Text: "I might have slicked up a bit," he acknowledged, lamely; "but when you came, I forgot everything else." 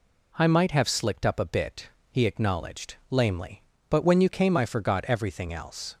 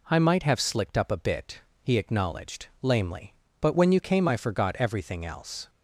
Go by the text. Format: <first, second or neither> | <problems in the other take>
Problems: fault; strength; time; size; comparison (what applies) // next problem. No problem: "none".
neither | none